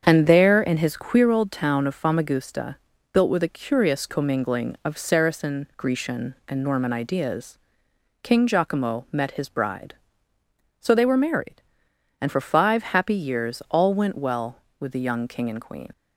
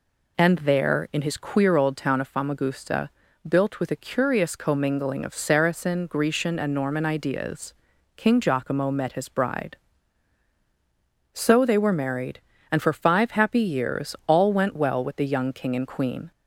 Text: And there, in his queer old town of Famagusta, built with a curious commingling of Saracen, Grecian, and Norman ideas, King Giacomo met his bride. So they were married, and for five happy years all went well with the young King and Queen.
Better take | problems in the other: second | starts louder than the rest; strong; until 1.0 s; 7.5 dB // leaves "Queen" unfinished; at 15.9 s; 65 ms

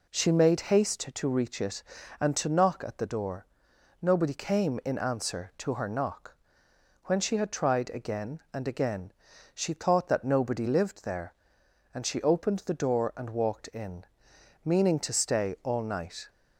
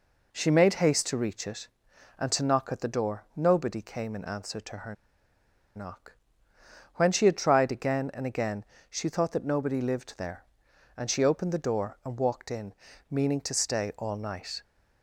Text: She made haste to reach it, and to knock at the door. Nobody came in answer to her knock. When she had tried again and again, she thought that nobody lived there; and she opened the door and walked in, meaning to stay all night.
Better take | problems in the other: first | pauses between "her" and "knock"; noticeable; at 4.9 s; 0.81 s long

